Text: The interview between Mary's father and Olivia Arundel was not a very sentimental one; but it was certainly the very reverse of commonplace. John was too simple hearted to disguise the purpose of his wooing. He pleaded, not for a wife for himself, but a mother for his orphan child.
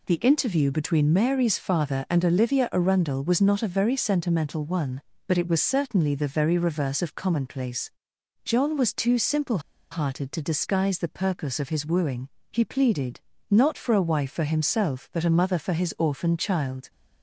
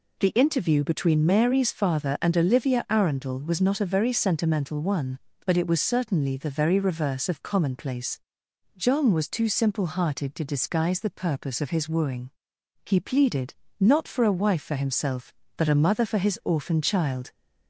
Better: second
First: pauses between "simple" and "hearted"; slight; at 9.5 s; 0.32 s long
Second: none

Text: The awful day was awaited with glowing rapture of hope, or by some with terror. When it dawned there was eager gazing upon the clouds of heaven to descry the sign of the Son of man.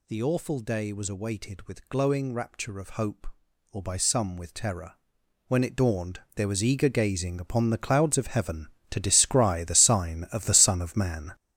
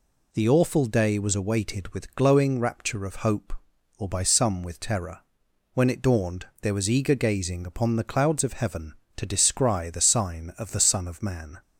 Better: second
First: gets louder; strong; throughout; 9.5 dB // pauses between "dawned" and "there"; slight; at 6.1 s; 0.16 s long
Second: pauses between "dawned" and "there"; slight; at 6.4 s; 0.16 s long

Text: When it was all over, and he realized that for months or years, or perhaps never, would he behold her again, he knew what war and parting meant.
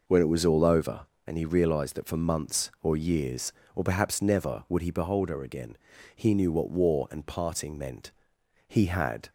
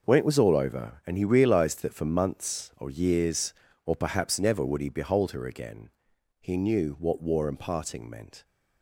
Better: second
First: goes on to say "He had"; noticeable; from 8.6 s on; 0.62 s long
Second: none

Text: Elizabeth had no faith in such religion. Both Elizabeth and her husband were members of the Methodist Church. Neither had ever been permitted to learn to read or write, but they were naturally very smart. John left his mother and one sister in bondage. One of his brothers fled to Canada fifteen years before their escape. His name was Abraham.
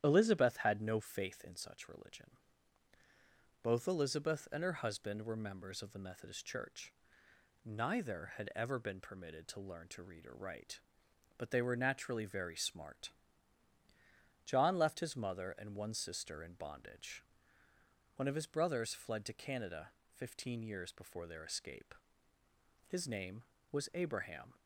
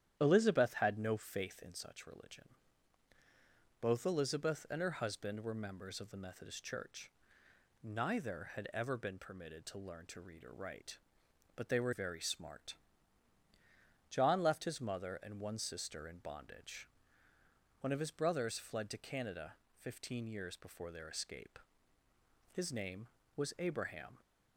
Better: first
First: starts louder than the rest; strong; until 1.0 s; 10.5 dB // pauses between "Canada" and "fifteen"; slight; at 19.8 s; 0.26 s long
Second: starts louder than the rest; strong; until 1.2 s; 10.5 dB // skips "naturally"; at 11.9 s // pauses between "Canada" and "fifteen"; slight; at 19.5 s; 0.26 s long

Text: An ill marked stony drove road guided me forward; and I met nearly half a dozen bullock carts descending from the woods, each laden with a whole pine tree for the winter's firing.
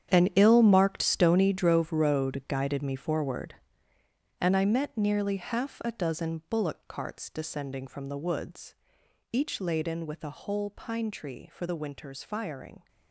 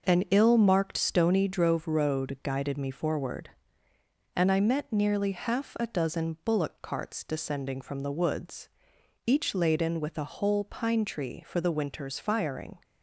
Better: second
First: gets quieter; strong; throughout; 14 dB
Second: none

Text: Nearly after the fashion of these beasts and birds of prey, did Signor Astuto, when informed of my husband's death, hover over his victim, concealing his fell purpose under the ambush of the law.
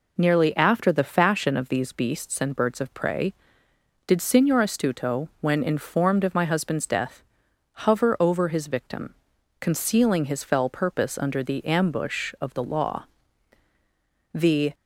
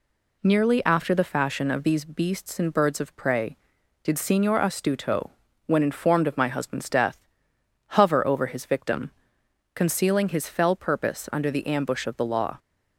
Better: second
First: goes on to say "The"; slight; from 14.3 s on; 0.40 s long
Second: none

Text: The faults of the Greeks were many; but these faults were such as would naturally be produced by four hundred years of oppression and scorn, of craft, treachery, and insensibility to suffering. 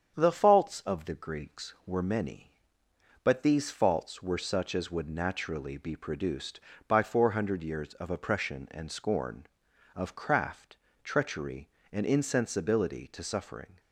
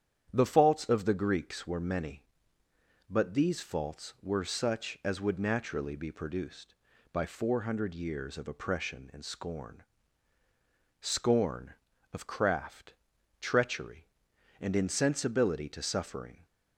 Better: first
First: starts louder than the rest; strong; until 1.2 s; 8 dB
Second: starts louder than the rest; strong; until 1.3 s; 9 dB // says "scorn" twice; at 11.0 s

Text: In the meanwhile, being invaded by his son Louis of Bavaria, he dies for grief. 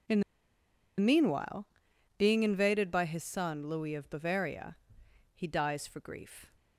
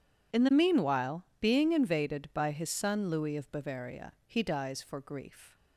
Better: second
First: pauses between "In" and "the"; noticeable; at 0.2 s; 0.77 s long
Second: none

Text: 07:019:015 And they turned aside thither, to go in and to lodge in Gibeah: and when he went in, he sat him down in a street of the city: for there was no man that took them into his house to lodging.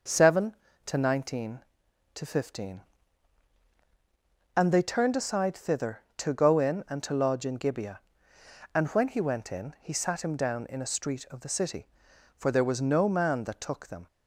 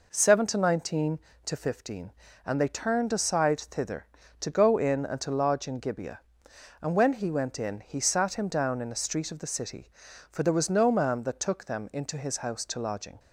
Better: second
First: stops before "into his house to lodging"; at 14.0 s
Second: none

